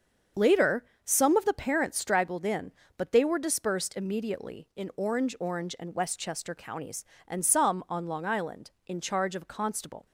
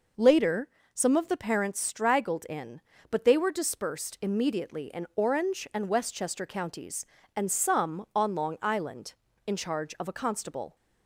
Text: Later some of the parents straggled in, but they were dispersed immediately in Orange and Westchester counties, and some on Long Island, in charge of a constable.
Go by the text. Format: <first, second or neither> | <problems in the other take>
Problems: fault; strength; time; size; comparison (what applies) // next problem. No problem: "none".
second | starts louder than the rest; until 1.5 s; 7 dB // pauses between "Later" and "some"; slight; at 0.8 s; 0.20 s long; slight in the second // says "Orange" twice; at 5.3 s